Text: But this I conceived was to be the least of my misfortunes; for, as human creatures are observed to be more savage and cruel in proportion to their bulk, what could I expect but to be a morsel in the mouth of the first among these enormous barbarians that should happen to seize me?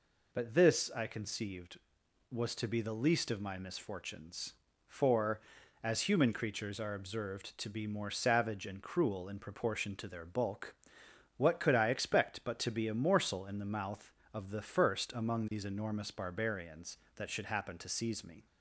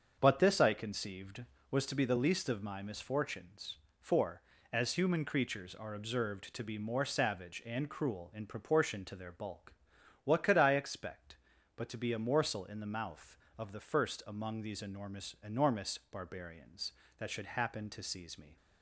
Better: first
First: none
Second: starts louder than the rest; until 1.2 s; 7 dB // says "enormous" twice; at 15.4 s

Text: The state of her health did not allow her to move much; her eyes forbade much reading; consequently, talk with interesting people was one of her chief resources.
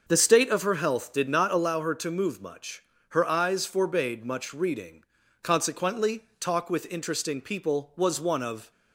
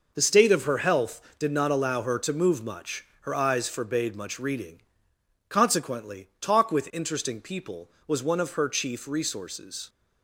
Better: second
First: starts louder than the rest; noticeable; until 1.0 s; 6 dB // stops before "her chief resources"; at 8.7 s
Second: none

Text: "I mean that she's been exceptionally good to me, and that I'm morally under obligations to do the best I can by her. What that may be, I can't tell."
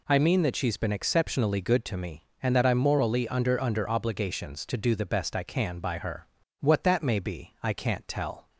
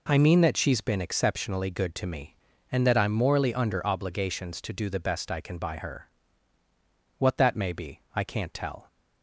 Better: second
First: says "under" twice; at 3.6 s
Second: none

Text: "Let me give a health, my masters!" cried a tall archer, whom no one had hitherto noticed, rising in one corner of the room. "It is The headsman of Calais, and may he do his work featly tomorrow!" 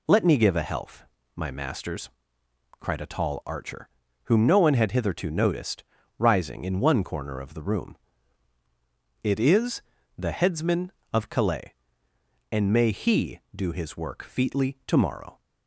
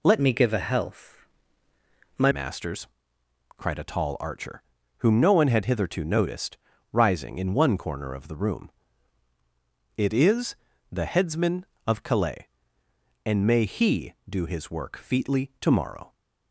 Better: first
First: pauses between "is" and "The"; slight; at 9.8 s; 0.36 s long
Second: changes voice from "me" to "my"; from 0.2 to 2.3 s; 2.1 s long // pauses between "is" and "The"; slight; at 10.5 s; 0.36 s long

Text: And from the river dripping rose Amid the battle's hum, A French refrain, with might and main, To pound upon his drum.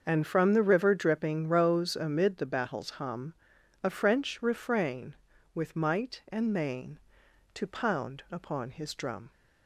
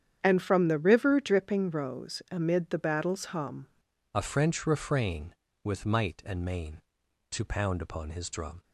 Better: first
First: starts louder than the rest; until 1.0 s; 6.5 dB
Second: starts louder than the rest; strong; until 1.2 s; 8.5 dB // changes voice at "A"; from 4.1 s on; 4.5 s long

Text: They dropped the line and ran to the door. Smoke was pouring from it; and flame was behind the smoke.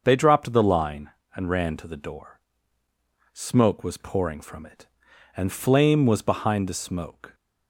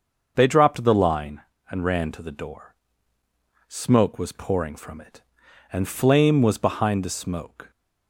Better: neither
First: starts louder than the rest; until 1.0 s; 6.5 dB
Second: starts louder than the rest; until 1.3 s; 6.5 dB

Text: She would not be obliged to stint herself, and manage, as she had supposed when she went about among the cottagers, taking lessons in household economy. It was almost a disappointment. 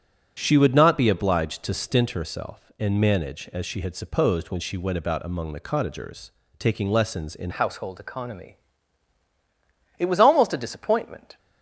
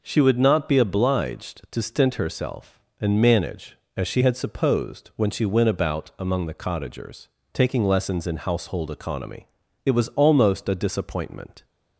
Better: second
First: starts louder than the rest; strong; until 1.4 s; 8.5 dB // changes voice at "household"; from 7.5 s on; 3.8 s long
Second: none

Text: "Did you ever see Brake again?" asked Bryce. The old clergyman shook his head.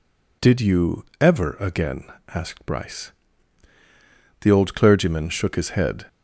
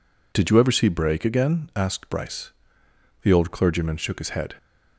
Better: second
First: pauses between "you" and "ever"; slight; at 1.0 s; 0.16 s long // skips "see Brake"; at 1.5 s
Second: none

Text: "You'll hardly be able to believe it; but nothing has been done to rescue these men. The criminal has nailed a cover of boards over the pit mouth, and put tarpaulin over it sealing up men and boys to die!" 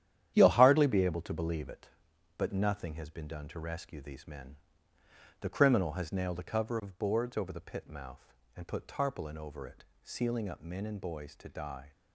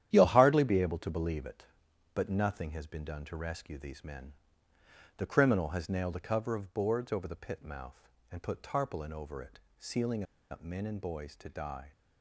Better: first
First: starts louder than the rest; strong; until 1.3 s; 11 dB // pauses between "it" and "sealing"; slight; at 9.8 s; 0.18 s long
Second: starts louder than the rest; strong; until 1.1 s; 11 dB // pauses between "it" and "sealing"; slight; at 9.6 s; 0.18 s long // pauses between "sealing" and "up"; slight; at 10.2 s; 0.28 s long

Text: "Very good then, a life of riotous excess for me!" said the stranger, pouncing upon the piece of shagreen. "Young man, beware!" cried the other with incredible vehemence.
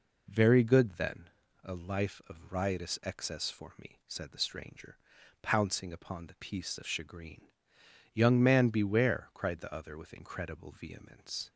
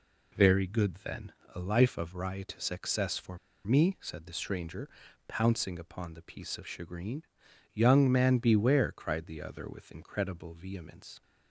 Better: first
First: none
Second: pauses between "for" and "me"; slight; at 3.3 s; 0.27 s long

